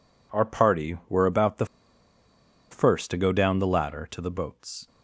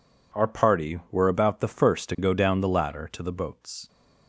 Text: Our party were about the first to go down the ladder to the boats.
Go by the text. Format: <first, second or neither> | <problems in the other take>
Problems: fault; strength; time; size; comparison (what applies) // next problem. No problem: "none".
second | pauses between "the" and "first"; at 1.6 s; 1.0 s long